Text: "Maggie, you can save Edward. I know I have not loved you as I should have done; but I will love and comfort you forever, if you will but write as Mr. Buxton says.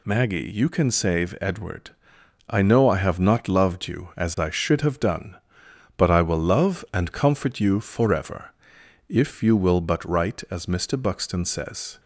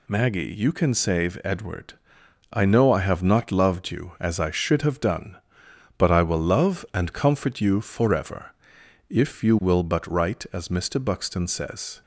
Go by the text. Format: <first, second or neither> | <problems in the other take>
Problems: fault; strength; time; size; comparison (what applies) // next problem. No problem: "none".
neither | none